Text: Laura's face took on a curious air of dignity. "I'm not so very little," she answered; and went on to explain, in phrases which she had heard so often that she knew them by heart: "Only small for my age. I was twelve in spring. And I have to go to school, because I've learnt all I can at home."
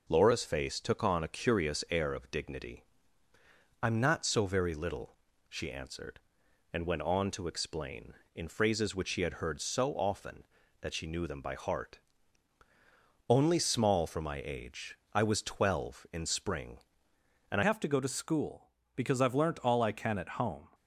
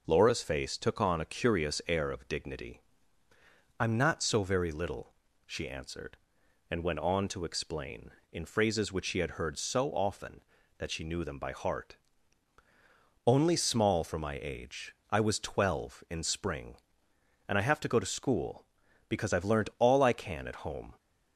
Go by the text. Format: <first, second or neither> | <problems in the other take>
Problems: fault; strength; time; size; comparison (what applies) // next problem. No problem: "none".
second | changes voice at "have"; from 17.6 s on; 3.0 s long